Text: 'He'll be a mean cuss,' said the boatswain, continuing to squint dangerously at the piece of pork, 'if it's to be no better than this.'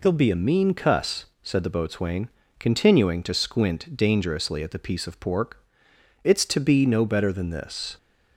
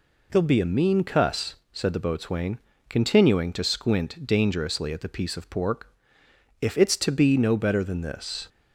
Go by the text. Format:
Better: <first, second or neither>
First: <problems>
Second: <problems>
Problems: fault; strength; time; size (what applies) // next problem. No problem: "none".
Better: second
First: skips "if"; at 5.9 s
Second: none